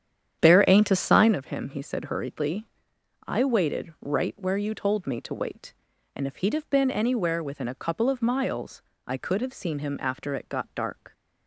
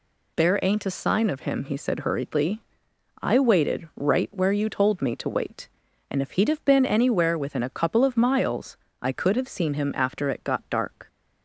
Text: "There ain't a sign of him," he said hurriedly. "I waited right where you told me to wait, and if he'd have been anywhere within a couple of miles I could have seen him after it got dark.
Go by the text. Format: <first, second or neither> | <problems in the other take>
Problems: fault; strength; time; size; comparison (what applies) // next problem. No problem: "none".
second | starts louder than the rest; strong; until 1.4 s; 9 dB // pauses between "miles" and "I"; slight; at 8.8 s; 0.24 s long; slight in the second